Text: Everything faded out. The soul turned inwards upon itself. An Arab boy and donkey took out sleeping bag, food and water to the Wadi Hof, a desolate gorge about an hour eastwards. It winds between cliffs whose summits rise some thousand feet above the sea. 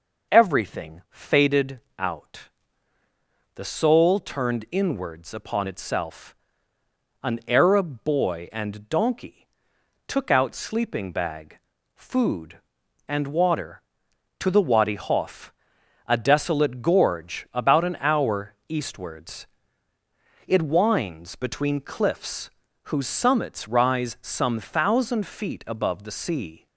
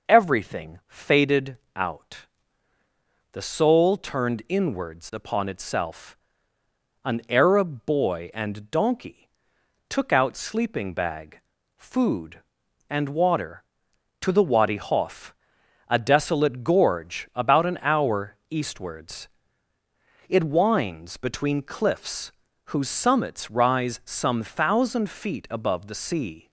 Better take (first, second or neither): neither